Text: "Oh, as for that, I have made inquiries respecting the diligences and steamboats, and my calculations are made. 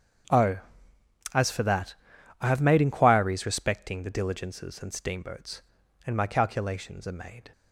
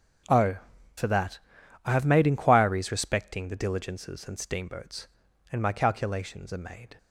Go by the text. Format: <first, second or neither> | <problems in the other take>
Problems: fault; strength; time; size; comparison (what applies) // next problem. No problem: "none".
first | starts louder than the rest; strong; until 2.1 s; 7.5 dB; strong in the first // skips "as"; at 0.7 s